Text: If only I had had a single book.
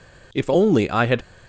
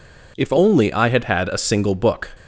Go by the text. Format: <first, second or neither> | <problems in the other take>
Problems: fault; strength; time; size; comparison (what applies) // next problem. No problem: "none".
second | stops before "had a single book"; at 1.2 s